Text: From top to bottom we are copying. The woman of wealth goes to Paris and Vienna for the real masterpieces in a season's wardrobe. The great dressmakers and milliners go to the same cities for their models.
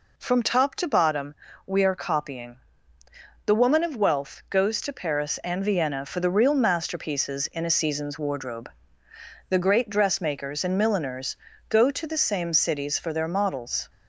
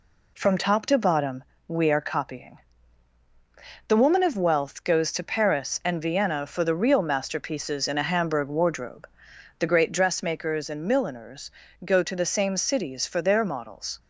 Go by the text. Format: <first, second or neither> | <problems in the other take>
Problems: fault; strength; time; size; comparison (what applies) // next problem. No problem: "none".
first | pauses between "bottom" and "we"; slight; at 1.4 s; 0.24 s long; slight in the first // says "hamburg" for "season's"; at 8.0 s // pauses between "milliners" and "go"; slight; at 11.5 s; 0.32 s long; slight in the first